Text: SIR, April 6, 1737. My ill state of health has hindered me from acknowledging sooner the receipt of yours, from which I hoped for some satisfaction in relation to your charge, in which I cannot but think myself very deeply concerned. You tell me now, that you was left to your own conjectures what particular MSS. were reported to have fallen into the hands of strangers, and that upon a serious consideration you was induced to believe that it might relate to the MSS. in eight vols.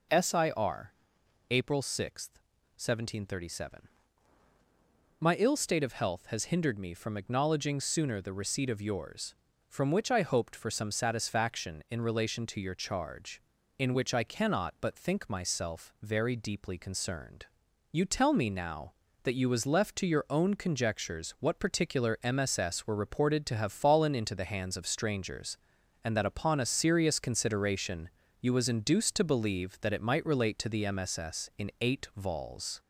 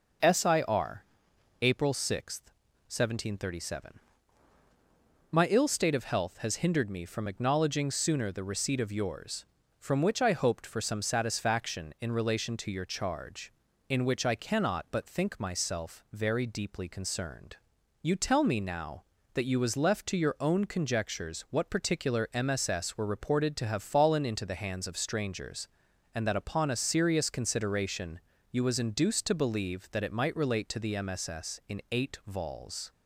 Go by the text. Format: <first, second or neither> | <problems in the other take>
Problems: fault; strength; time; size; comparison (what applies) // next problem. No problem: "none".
second | gets louder; slight; throughout; 2.5 dB // pauses between "consideration" and "you"; slight; at 28.0 s; 0.32 s long; slight in the second